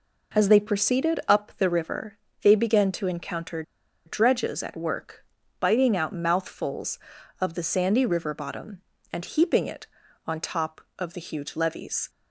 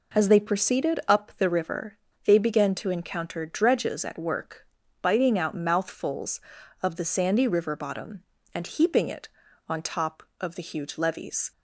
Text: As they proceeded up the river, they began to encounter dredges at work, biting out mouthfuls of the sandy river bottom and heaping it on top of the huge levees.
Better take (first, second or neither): second